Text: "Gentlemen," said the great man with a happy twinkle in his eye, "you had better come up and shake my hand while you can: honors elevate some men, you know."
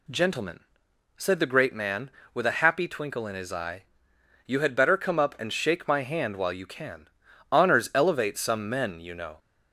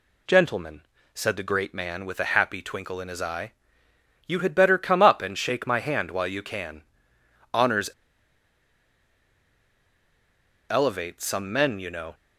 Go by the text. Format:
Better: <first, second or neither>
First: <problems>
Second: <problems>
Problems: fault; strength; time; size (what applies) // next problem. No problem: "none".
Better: first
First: none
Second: pauses between "honors" and "elevate"; strong; at 7.8 s; 2.8 s long